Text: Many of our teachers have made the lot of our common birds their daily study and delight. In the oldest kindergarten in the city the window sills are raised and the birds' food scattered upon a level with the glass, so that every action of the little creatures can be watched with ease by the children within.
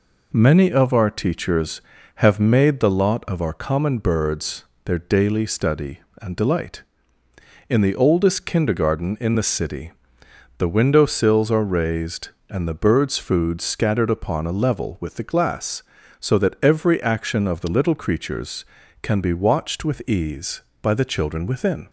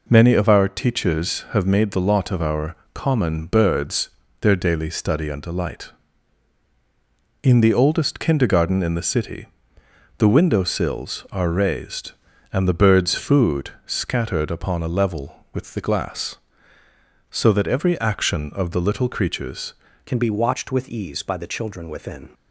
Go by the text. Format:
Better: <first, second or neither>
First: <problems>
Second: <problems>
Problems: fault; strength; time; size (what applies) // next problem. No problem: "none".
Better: first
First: pauses between "birds" and "their"; slight; at 4.6 s; 0.20 s long // pauses between "city" and "the"; noticeable; at 9.9 s; 0.66 s long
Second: pauses between "our" and "common"; slight; at 2.7 s; 0.18 s long // pauses between "birds" and "their"; slight; at 4.0 s; 0.32 s long // pauses between "city" and "the"; noticeable; at 9.4 s; 0.72 s long // pauses between "food" and "scattered"; slight; at 13.7 s; 0.16 s long // changes voice at "can"; from 20.0 s on; 2.2 s long